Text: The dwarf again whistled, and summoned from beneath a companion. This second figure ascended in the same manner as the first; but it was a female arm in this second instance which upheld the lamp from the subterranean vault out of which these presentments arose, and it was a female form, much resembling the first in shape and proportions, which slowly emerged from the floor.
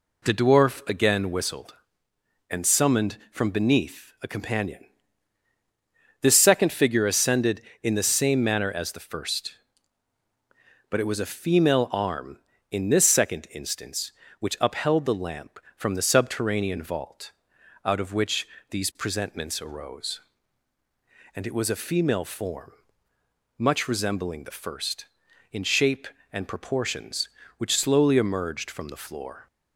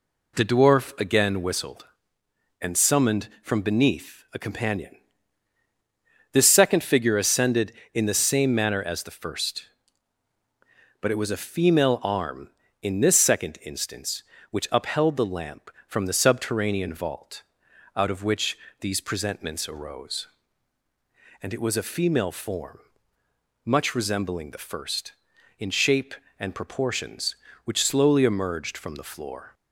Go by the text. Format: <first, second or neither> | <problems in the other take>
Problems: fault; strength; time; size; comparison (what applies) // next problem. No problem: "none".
neither | pauses between "vault" and "out"; noticeable; the same in both // pauses between "which" and "these"; slight; the same in both